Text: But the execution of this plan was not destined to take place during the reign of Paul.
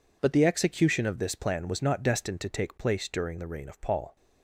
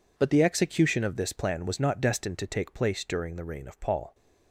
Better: neither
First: none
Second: none

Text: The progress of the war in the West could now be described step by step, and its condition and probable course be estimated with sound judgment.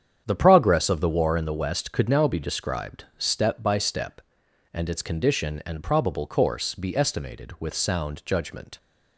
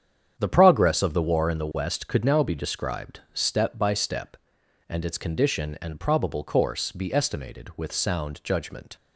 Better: neither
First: starts louder than the rest; strong; until 1.2 s; 8.5 dB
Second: starts louder than the rest; strong; until 1.3 s; 8.5 dB

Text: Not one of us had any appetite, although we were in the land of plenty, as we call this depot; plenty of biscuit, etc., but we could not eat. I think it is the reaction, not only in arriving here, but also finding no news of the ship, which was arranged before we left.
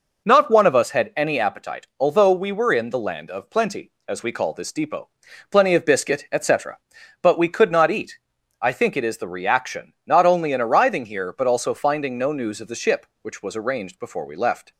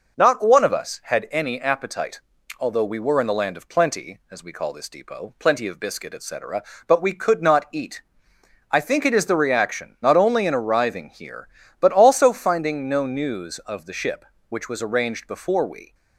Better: first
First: none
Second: stops before "left"; at 15.9 s

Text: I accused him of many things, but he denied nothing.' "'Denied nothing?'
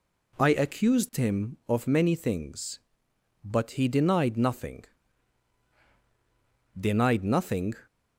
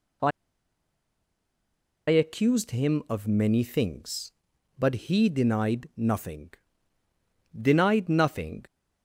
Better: first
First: none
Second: pauses between "I" and "accused"; strong; at 0.3 s; 1.7 s long

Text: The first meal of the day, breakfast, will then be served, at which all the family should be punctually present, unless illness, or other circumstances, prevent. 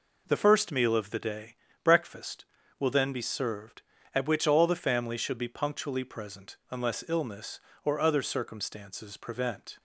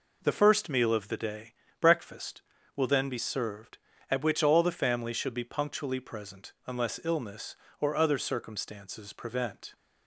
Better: neither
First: none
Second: none

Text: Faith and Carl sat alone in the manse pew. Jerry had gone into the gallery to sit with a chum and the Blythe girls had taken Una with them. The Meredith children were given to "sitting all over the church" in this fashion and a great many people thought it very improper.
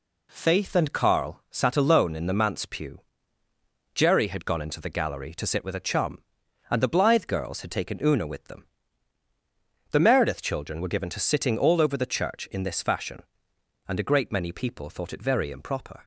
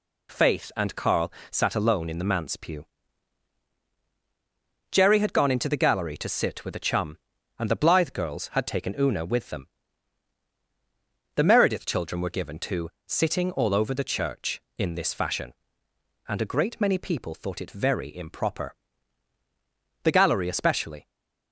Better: first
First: none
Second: pauses between "Carl" and "sat"; slight; at 1.3 s; 0.18 s long // pauses between "to" and "sitting"; slight; at 12.8 s; 0.18 s long // goes on to say "The gallery especially"; noticeable; from 20.0 s on; 1.0 s long // stays silent after the last word; slight; from 21.0 s on; 0.5 s long

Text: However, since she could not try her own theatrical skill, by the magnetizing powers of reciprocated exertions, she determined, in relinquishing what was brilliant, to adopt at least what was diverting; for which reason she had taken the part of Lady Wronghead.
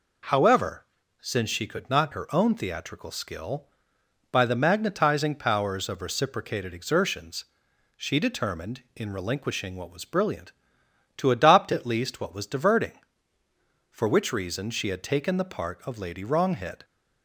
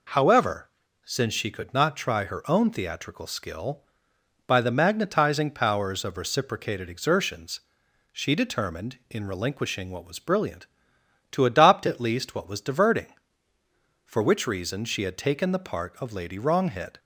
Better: second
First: skips "try"; at 2.1 s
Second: none

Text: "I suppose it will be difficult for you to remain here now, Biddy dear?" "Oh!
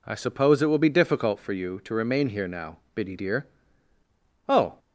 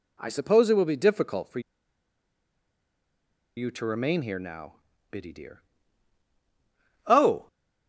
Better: first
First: none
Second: pauses between "for" and "you"; strong; at 1.6 s; 1.9 s long

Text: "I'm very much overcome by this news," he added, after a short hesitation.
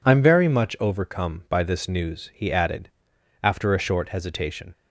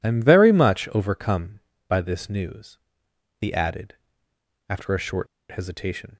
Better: first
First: none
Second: pauses between "short" and "hesitation"; slight; at 5.2 s; 0.23 s long

